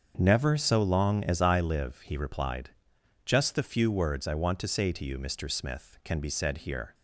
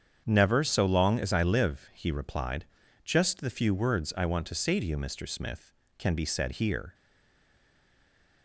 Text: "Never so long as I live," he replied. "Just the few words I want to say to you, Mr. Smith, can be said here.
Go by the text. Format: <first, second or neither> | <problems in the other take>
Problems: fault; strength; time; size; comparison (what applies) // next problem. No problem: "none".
first | starts louder than the rest; strong; until 1.2 s; 7.5 dB; also in the first // stays silent after the last word; noticeable; from 6.9 s on; 1.5 s long